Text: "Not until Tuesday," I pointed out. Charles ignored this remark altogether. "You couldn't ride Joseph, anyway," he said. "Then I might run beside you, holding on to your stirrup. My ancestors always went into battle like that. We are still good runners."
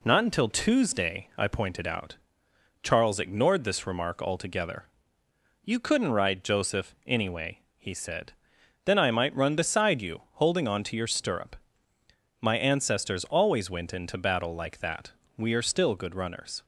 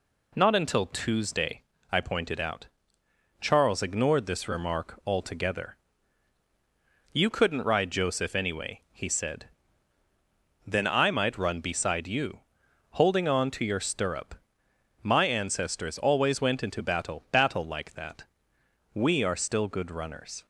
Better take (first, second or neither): first